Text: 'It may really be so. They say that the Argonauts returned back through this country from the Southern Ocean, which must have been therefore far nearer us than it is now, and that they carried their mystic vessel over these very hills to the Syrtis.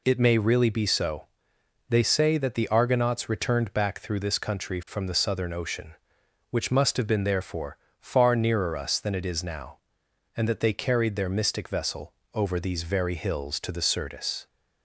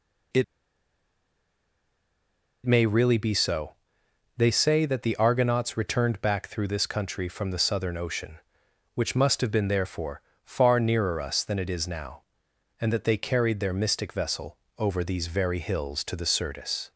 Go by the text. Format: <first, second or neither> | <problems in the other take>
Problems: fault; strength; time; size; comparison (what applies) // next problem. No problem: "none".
first | pauses between "It" and "may"; strong; at 0.4 s; 2.2 s long // pauses between "therefore" and "far"; slight; at 10.2 s; 0.22 s long; slight in the first // pauses between "vessel" and "over"; slight; at 14.5 s; 0.20 s long; slight in the first